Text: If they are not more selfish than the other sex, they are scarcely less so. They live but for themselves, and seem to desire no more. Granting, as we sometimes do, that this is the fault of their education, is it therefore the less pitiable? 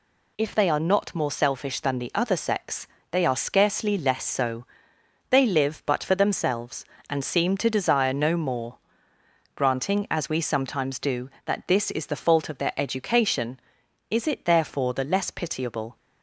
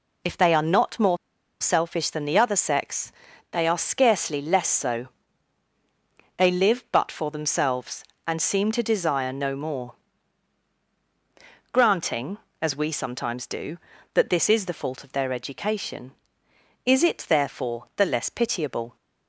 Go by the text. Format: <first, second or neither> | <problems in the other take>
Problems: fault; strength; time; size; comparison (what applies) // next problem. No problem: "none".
first | pauses between "more" and "selfish"; at 1.1 s; 0.44 s long